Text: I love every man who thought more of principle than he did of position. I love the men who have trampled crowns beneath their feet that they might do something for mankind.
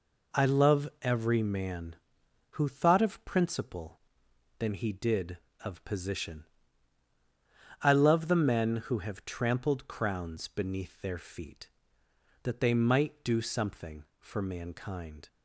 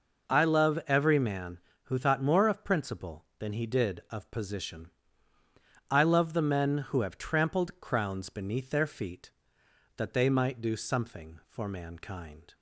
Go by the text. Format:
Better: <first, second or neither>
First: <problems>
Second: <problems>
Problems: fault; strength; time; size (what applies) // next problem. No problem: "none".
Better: second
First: skips "more"; at 3.0 s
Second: none